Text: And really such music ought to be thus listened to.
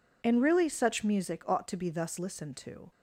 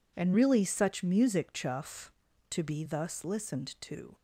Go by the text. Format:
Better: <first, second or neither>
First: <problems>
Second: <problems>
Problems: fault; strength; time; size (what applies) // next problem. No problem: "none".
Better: first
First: none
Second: says "chuff" for "ought"; at 1.5 s